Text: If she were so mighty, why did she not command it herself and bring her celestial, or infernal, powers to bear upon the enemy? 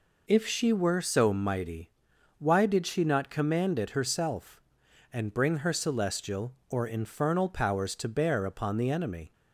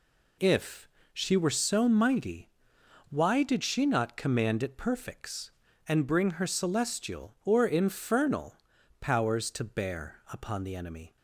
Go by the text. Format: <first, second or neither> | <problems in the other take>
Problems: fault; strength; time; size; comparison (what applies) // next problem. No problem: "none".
first | pauses between "If" and "she"; slight; at 0.8 s; 0.24 s long // says "perfects" for "herself"; at 4.7 s